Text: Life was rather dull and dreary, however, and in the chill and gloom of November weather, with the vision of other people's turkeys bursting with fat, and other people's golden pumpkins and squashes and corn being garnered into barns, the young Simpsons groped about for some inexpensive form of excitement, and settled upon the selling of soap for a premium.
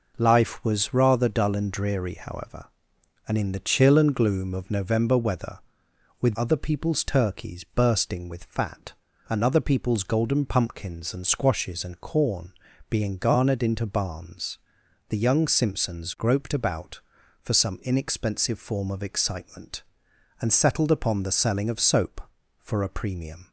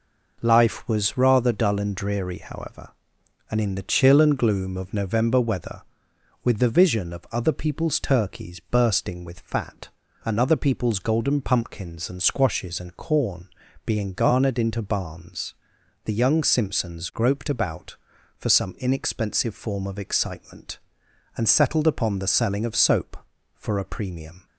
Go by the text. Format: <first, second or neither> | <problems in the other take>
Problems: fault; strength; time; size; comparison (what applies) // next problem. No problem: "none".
second | skips "the vision of"; at 6.3 s // pauses between "corn" and "being"; at 12.5 s; 0.38 s long; also in the second